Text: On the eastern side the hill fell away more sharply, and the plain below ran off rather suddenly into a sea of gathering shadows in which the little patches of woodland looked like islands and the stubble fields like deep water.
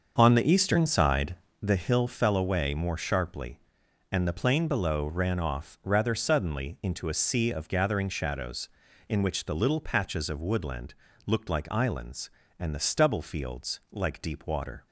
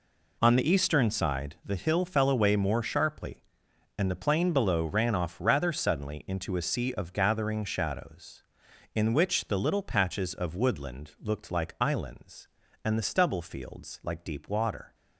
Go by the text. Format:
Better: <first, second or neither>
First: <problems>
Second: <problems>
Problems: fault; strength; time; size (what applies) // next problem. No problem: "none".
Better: second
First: starts louder than the rest; until 1.7 s; 6.5 dB // pauses between "side" and "the"; slight; at 1.3 s; 0.26 s long // pauses between "woodland" and "looked"; slight; at 10.9 s; 0.32 s long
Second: none